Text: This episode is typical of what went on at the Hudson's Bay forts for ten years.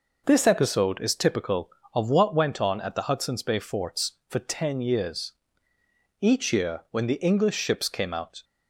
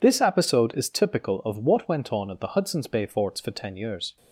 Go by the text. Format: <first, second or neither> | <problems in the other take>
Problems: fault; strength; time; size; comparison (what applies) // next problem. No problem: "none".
second | goes on to say "Each year when the English ships came out"; strong; from 6.2 s on; 2.2 s long